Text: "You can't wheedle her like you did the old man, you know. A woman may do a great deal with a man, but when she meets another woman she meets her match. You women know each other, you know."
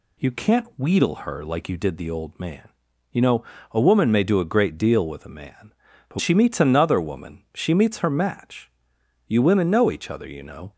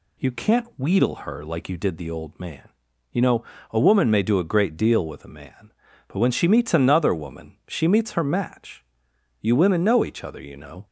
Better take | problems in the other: second | skips "when"; at 6.1 s

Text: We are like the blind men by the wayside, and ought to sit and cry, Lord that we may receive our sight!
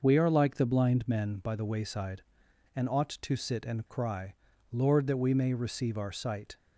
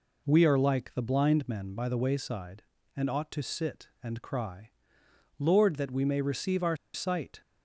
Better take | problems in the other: first | pauses between "our" and "sight"; slight; at 6.7 s; 0.18 s long

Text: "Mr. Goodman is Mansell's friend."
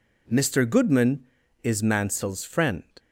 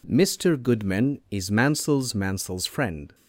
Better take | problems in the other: first | says "Mansell's" twice; at 2.1 s

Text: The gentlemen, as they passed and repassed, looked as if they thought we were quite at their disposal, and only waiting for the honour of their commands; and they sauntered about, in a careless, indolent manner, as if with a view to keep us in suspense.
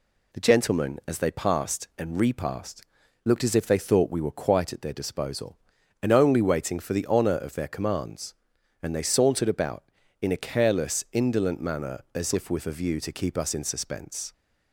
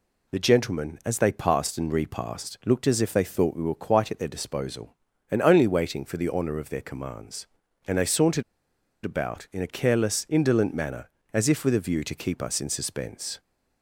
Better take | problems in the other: first | pauses between "sauntered" and "about"; noticeable; at 8.4 s; 0.60 s long

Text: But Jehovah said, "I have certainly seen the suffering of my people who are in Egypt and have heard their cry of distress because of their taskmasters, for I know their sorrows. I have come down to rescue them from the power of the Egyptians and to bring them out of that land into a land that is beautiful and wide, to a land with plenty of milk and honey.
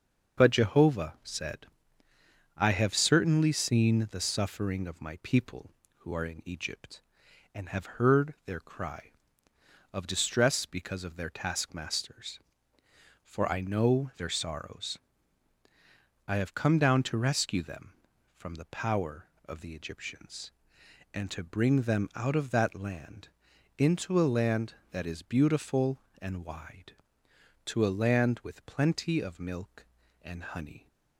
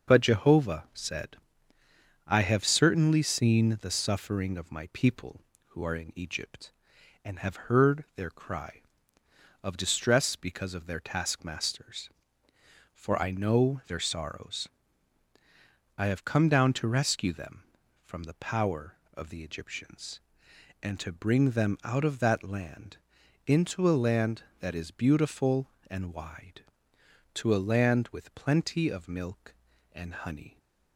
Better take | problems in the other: neither | starts louder than the rest; the same in both // pauses between "land" and "into"; noticeable; the same in both

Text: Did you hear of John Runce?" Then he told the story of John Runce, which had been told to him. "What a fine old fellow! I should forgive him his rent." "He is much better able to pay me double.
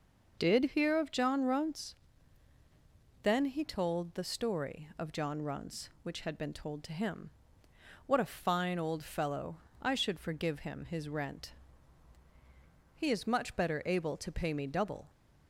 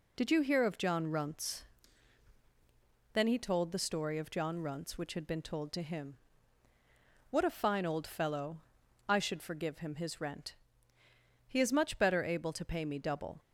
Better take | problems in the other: second | skips "you"; at 0.7 s

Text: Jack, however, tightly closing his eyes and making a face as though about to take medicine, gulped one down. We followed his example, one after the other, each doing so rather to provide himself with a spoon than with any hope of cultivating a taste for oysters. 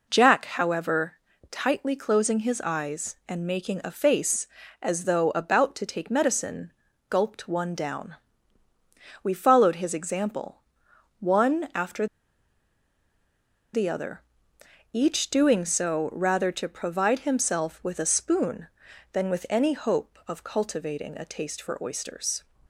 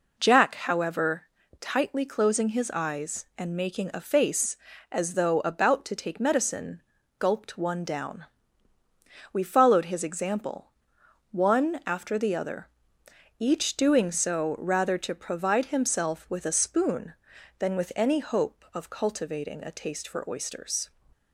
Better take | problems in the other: second | pauses between "after" and "the"; strong; at 12.0 s; 1.6 s long

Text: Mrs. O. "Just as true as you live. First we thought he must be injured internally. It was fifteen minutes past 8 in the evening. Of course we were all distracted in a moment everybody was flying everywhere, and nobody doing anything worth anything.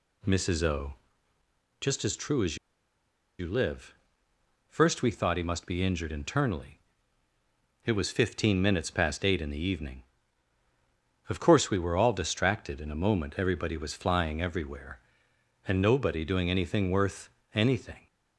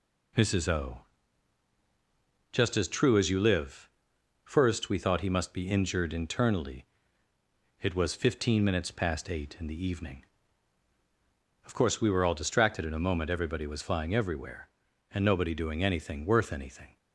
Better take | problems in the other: second | pauses between "as" and "you"; noticeable; at 2.5 s; 0.83 s long // pauses between "worth" and "anything"; slight; at 17.3 s; 0.22 s long

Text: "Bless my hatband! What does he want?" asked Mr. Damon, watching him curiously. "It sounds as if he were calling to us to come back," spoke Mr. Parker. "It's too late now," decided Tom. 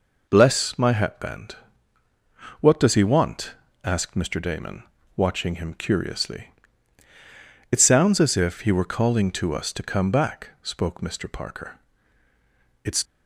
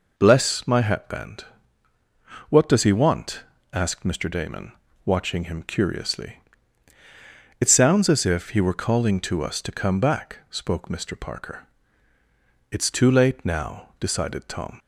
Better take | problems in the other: second | stops before "too late now decided Tom"; at 13.0 s

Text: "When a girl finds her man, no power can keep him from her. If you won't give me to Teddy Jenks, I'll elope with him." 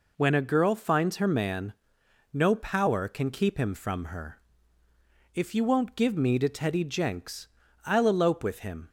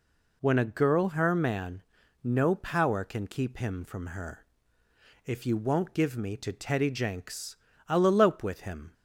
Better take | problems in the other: first | skips "finds"; at 1.0 s

